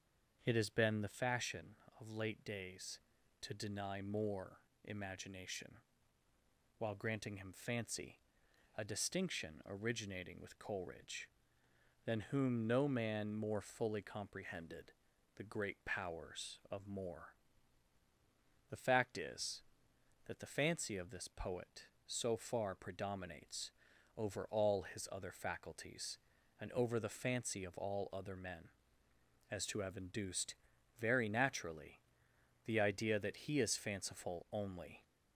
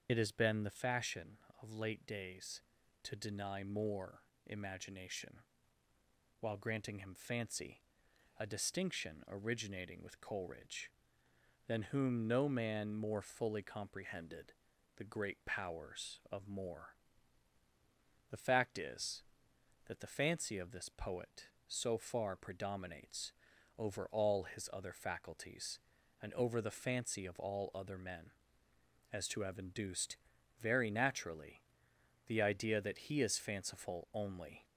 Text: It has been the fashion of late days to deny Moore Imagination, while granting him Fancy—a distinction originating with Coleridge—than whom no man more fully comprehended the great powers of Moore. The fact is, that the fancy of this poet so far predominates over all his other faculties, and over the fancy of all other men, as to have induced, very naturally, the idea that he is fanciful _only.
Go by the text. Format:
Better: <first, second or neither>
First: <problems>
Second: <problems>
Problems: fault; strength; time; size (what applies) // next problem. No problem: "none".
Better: first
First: starts louder than the rest; until 1.4 s; 7 dB // pauses between "Moore" and "Imagination"; slight; at 4.5 s; 0.26 s long // pauses between "comprehended" and "the"; at 14.9 s; 0.44 s long // pauses between "predominates" and "over"; at 23.7 s; 0.44 s long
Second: loses the start of "It"; at 0.0 s; 65 ms // starts louder than the rest; until 1.1 s; 7 dB // pauses between "Moore" and "Imagination"; slight; at 4.2 s; 0.26 s long // pauses between "comprehended" and "the"; at 14.5 s; 0.44 s long // pauses between "predominates" and "over"; at 23.3 s; 0.44 s long